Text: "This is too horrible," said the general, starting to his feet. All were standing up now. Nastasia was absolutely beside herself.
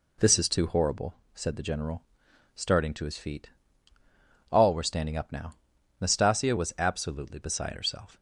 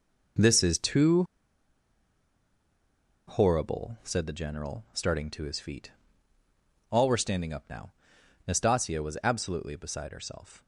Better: first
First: none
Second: pauses between "too" and "horrible"; strong; at 1.2 s; 2.0 s long

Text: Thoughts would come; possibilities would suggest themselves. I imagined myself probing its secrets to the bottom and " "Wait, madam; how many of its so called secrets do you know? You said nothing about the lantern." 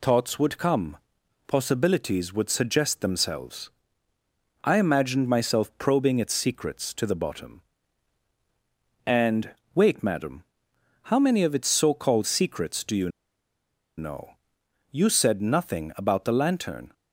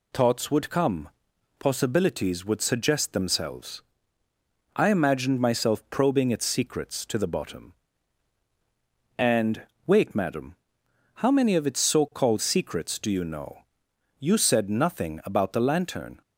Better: second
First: pauses between "you" and "know"; noticeable; at 13.0 s; 0.89 s long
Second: none

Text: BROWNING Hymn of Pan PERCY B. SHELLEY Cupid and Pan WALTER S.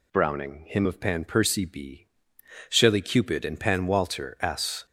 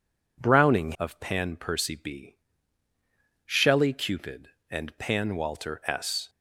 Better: first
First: none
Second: skips "Hymn"; at 0.9 s

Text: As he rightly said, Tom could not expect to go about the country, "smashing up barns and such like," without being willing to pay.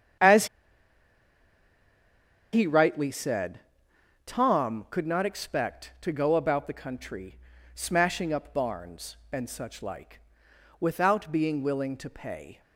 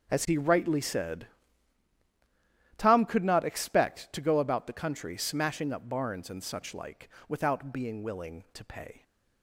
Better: second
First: starts louder than the rest; strong; until 3.2 s; 8.5 dB // pauses between "As" and "he"; strong; at 0.4 s; 2.0 s long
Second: starts louder than the rest; until 1.1 s; 6.5 dB

